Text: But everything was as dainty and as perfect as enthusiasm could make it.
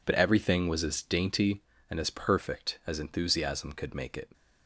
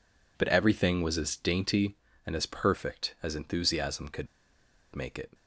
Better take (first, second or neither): first